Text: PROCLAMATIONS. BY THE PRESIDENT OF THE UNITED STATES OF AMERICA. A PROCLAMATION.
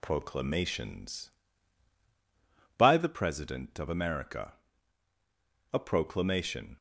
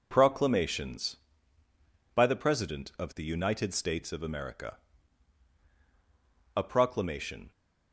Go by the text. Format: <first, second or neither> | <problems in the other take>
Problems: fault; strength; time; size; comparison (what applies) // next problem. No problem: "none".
second | skips "OF THE UNITED STATES"; at 3.7 s